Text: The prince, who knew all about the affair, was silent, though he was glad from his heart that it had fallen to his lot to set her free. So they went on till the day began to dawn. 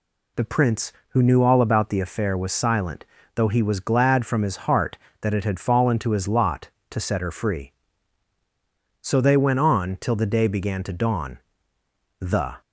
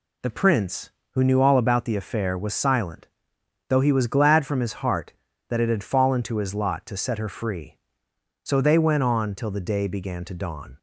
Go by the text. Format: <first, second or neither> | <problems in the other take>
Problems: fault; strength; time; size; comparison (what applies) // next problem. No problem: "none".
second | goes on to say "The"; slight; from 12.1 s on; 0.42 s long